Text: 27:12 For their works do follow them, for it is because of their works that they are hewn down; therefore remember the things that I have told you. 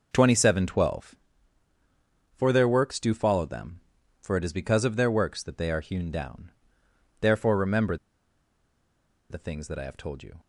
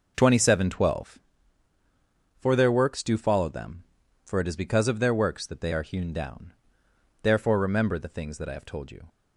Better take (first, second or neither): second